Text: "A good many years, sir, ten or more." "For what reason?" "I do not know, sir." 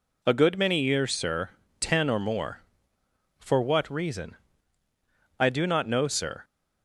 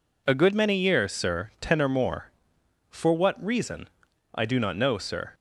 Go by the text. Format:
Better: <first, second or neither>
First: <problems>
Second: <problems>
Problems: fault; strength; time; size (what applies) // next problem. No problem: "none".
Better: neither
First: none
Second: none